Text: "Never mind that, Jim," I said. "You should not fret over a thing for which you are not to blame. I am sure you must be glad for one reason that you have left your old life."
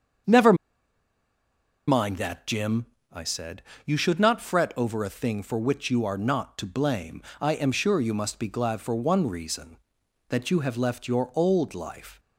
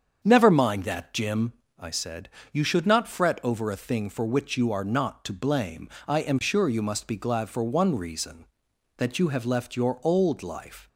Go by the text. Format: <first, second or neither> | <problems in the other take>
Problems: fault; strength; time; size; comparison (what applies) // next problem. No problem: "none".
second | starts louder than the rest; strong; until 2.6 s; 7.5 dB; strong in the second // pauses between "Never" and "mind"; strong; at 0.5 s; 1.3 s long